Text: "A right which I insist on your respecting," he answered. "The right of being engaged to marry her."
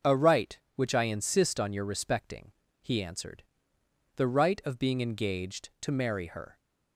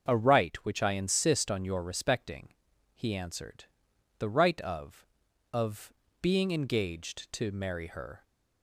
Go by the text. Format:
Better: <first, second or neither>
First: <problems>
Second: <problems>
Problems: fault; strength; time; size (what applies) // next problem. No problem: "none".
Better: first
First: starts louder than the rest; until 1.2 s; 6 dB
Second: starts louder than the rest; until 1.1 s; 6.5 dB // says "of" twice; at 5.5 s